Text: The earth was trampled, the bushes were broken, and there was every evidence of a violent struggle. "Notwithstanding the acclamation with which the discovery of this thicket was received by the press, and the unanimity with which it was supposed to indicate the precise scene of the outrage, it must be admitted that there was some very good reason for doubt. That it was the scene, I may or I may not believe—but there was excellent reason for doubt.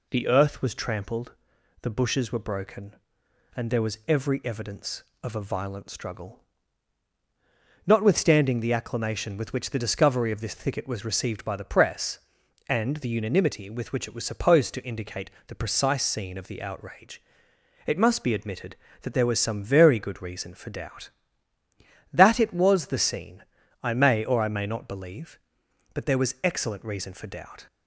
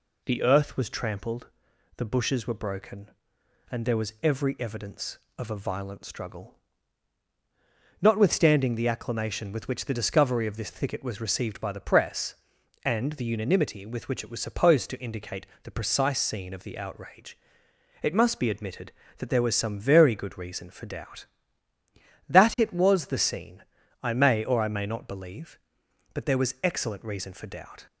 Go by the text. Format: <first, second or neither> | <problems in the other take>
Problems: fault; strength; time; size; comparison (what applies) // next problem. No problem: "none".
neither | pauses between "indicate" and "the"; slight; the same in both